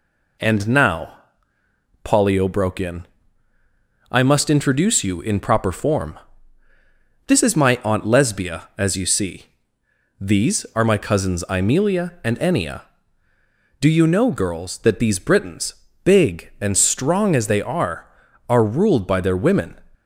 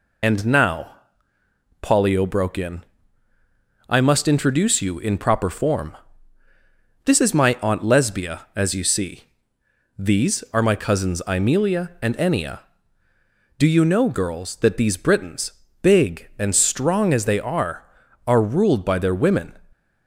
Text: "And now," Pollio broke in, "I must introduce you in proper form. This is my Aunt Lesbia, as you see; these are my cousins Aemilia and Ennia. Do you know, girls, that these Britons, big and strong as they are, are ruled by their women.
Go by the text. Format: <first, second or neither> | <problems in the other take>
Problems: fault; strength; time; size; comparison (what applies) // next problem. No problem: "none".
first | loses the start of "And"; at 0.2 s; 50 ms